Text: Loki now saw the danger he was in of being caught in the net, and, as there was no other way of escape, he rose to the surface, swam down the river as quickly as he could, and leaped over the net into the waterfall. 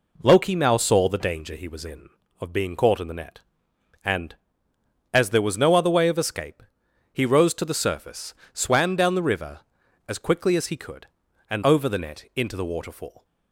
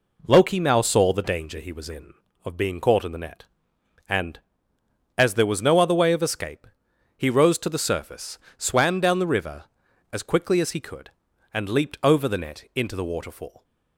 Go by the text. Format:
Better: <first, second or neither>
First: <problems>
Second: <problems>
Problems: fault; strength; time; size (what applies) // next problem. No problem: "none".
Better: second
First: skips "leaped"; at 11.6 s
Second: none